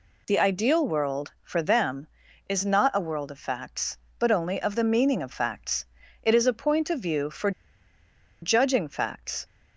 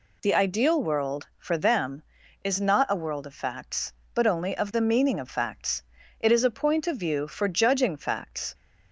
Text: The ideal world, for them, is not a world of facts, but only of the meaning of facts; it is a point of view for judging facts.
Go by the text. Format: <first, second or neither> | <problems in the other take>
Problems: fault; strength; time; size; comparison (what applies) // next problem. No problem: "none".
second | pauses between "for" and "judging"; noticeable; at 7.5 s; 0.91 s long